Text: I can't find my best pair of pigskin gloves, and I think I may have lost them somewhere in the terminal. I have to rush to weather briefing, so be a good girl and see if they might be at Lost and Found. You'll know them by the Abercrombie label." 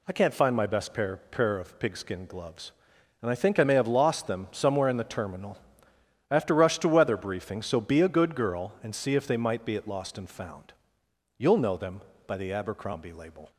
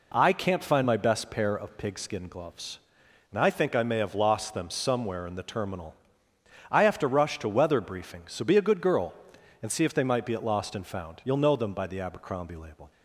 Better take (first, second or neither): second